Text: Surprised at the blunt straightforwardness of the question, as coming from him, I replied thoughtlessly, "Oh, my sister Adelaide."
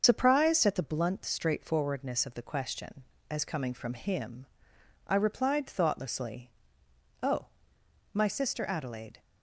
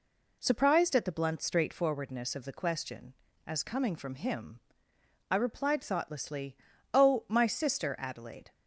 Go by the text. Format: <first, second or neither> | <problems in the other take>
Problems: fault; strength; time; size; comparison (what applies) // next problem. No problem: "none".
second | loses the start of "Surprised"; at 0.0 s; 80 ms // starts louder than the rest; until 1.0 s; 6.5 dB